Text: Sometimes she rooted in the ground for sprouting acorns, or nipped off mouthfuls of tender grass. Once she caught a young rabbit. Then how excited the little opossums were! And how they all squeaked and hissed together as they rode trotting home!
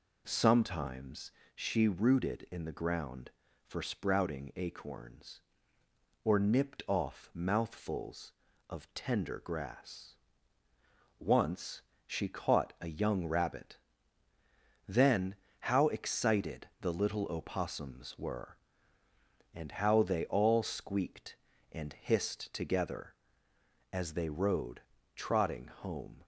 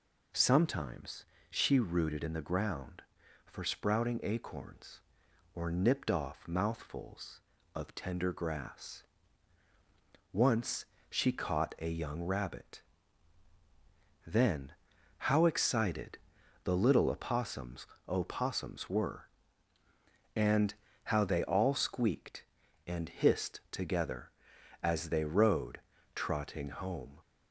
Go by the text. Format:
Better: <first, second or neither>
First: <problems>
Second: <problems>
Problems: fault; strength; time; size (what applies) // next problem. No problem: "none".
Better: first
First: pauses between "Sometimes" and "she"; slight; at 1.2 s; 0.24 s long // pauses between "Once" and "she"; slight; at 11.8 s; 0.26 s long // pauses between "Then" and "how"; slight; at 15.3 s; 0.24 s long // pauses between "rode" and "trotting"; slight; at 24.7 s; 0.34 s long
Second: pauses between "Sometimes" and "she"; slight; at 1.2 s; 0.24 s long // pauses between "Once" and "she"; slight; at 10.8 s; 0.24 s long // pauses between "Then" and "how"; noticeable; at 14.7 s; 0.46 s long // pauses between "excited" and "the"; noticeable; at 16.1 s; 0.48 s long // says "opossums" twice; at 18.0 s // pauses between "And" and "how"; slight; at 20.7 s; 0.32 s long // pauses between "rode" and "trotting"; slight; at 25.8 s; 0.34 s long